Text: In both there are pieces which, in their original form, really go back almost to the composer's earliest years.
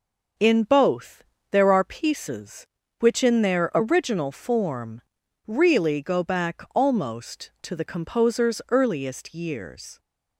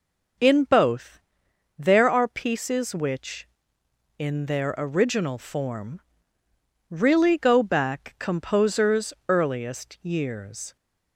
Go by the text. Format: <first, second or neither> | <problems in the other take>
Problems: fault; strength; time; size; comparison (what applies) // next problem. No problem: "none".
first | pauses between "both" and "there"; noticeable; at 1.1 s; 0.62 s long; slight in the first // skips "almost to the"; at 8.1 s // pauses between "composer's" and "earliest"; slight; at 9.1 s; 0.16 s long